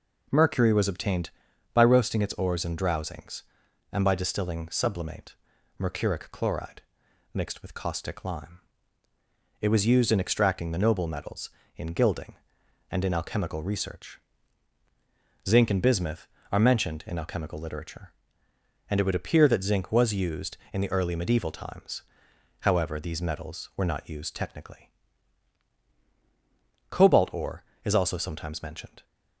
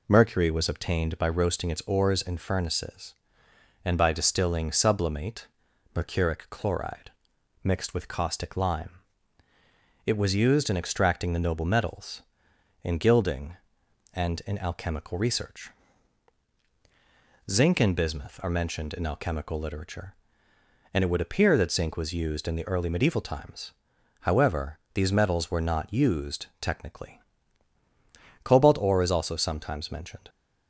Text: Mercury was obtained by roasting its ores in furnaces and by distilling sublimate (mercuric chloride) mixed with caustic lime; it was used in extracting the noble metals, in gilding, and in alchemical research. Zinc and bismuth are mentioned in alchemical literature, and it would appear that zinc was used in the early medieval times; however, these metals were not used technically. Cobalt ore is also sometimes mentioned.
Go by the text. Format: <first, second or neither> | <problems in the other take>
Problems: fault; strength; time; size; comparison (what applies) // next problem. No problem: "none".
second | says "drowsings" for "furnaces"; at 2.7 s